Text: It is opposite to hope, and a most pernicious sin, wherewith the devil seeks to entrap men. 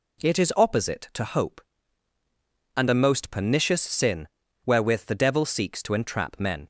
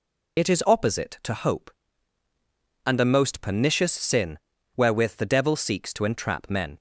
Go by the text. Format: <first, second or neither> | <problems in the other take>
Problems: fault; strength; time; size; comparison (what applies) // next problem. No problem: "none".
first | loses the start of "It"; at 0.3 s; 65 ms